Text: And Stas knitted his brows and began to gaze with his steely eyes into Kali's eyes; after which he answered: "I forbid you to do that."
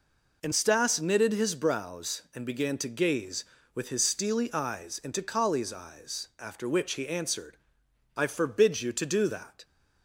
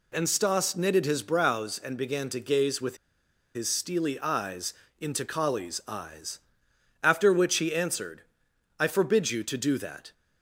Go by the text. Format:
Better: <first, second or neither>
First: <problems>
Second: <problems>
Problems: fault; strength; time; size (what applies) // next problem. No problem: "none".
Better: first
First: none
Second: pauses between "with" and "his"; noticeable; at 2.9 s; 0.59 s long // pauses between "eyes" and "into"; slight; at 4.7 s; 0.28 s long